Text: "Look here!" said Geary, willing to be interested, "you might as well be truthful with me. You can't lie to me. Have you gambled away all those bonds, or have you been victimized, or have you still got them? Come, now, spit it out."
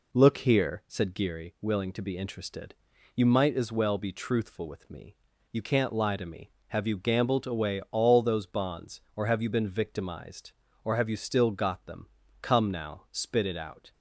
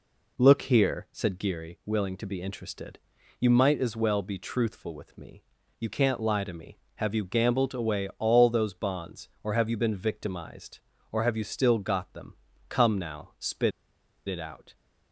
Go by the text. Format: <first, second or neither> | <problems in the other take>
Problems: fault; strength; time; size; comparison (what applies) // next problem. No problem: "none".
first | pauses between "spit" and "it"; noticeable; at 13.7 s; 0.56 s long